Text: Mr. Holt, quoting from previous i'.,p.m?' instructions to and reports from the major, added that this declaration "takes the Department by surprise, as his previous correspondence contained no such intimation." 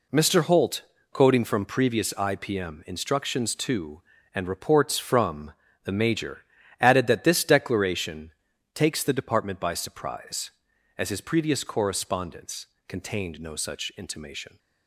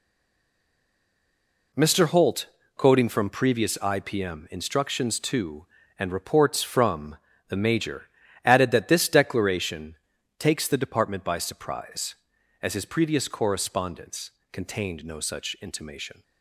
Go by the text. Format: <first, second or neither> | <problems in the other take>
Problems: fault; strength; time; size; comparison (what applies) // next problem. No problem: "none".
first | stays silent before the first word; noticeable; until 1.7 s; 1.7 s long // pauses between "from" and "the"; slight; at 7.1 s; 0.32 s long; slight in the first // pauses between "declaration" and "takes"; at 9.9 s; 0.44 s long; also in the first // pauses between "correspondence" and "contained"; slight; at 14.3 s; 0.18 s long; slight in the first